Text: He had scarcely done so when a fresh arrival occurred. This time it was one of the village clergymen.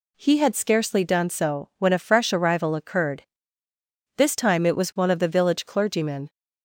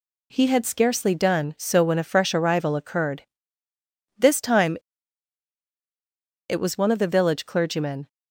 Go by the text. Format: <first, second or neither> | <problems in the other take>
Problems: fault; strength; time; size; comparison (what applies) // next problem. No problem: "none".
first | pauses between "time" and "it"; strong; at 4.7 s; 1.7 s long